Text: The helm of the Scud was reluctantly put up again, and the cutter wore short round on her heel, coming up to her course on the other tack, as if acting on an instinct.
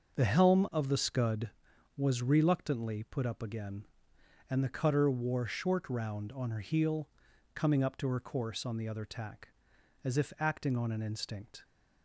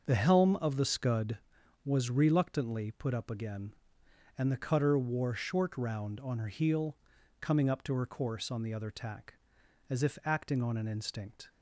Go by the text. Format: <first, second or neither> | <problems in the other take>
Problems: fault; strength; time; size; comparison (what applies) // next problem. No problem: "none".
neither | starts louder than the rest; the same in both